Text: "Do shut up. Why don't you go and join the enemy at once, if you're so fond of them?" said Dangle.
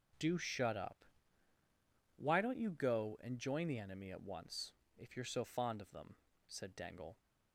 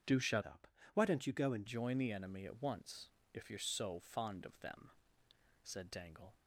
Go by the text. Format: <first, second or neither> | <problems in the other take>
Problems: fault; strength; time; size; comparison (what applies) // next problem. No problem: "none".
first | changes voice from "up" to "and"; from 0.4 to 1.6 s; 1.2 s long